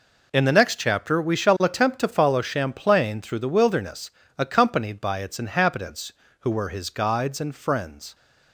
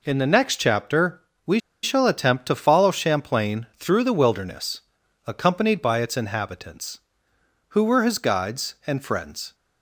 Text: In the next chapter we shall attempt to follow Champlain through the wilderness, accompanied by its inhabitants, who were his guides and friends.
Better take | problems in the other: first | pauses between "chapter" and "we"; slight; at 1.2 s; 0.24 s long // pauses between "we" and "shall"; slight; at 1.5 s; 0.23 s long

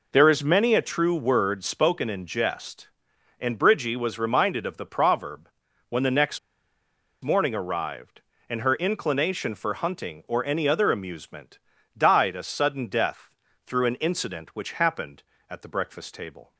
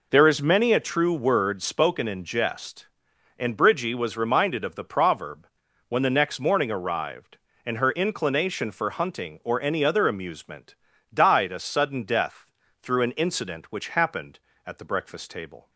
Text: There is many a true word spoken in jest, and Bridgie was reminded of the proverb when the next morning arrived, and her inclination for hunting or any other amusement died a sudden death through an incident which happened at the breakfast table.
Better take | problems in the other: second | pauses between "proverb" and "when"; at 5.4 s; 0.40 s long; also in the second // pauses between "next" and "morning"; noticeable; at 6.3 s; 0.84 s long // pauses between "amusement" and "died"; at 11.5 s; 0.40 s long; also in the second // pauses between "death" and "through"; slight; at 13.2 s; 0.36 s long; slight in the second

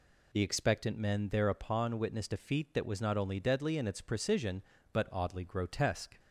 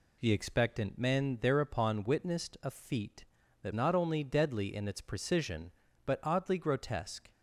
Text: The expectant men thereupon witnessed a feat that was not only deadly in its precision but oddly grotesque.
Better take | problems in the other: first | skips "was"; at 3.7 s

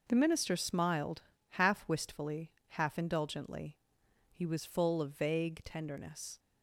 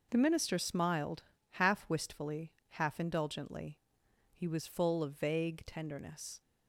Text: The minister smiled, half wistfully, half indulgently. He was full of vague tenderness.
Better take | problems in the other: neither | none

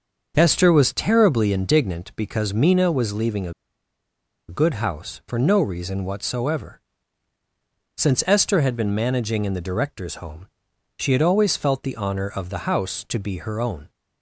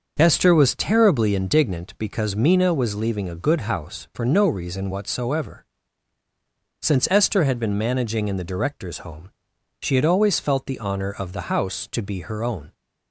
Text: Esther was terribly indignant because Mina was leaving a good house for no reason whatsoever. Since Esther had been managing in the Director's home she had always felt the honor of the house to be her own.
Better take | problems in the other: second | starts louder than the rest; until 1.3 s; 6.5 dB; also in the second // pauses between "a" and "good"; noticeable; at 3.5 s; 0.96 s long // pauses between "home" and "she"; noticeable; at 10.4 s; 0.50 s long; noticeable in the second

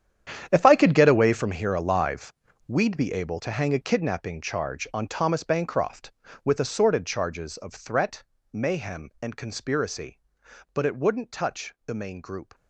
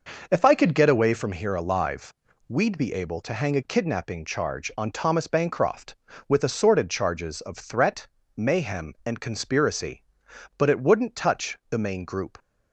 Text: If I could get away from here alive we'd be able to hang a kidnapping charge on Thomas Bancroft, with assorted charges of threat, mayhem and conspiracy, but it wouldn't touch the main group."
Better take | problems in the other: second | gets quieter; strong; throughout; 15.5 dB // pauses between "alive" and "we'd"; slight; at 2.3 s; 0.34 s long; slight in the second

